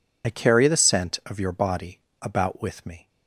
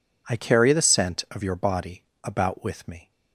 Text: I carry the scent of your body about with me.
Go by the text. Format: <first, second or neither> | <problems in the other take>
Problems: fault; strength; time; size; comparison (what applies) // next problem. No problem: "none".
second | loses the start of "I"; at 0.2 s; 50 ms // pauses between "body" and "about"; slight; at 1.9 s; 0.21 s long; slight in the second